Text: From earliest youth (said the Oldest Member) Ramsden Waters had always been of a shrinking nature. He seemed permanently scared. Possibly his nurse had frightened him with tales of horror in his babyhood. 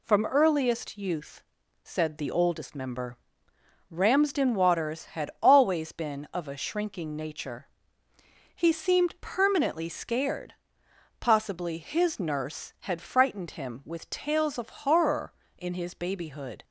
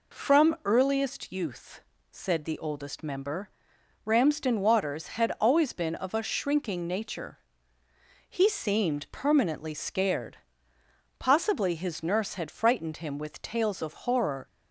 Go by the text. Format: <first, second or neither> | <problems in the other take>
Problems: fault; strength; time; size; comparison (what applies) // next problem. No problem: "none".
first | stops before "in his babyhood"; at 14.4 s